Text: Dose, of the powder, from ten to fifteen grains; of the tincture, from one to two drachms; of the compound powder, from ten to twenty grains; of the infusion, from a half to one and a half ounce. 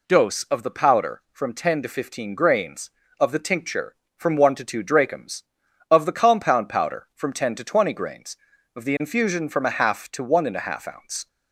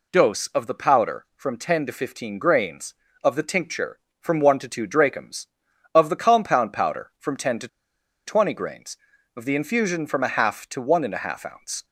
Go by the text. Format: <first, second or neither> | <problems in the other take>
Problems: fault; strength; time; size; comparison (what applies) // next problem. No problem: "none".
first | pauses between "to" and "twenty"; noticeable; at 7.6 s; 0.59 s long